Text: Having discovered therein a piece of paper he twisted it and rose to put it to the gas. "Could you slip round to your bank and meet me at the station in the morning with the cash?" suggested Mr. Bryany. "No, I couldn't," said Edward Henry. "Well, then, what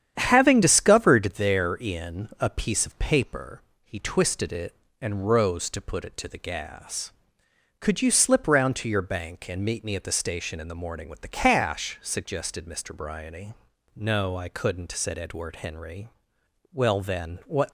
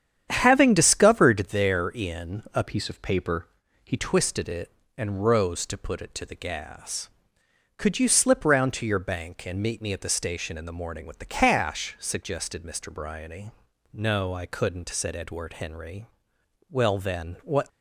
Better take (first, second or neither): first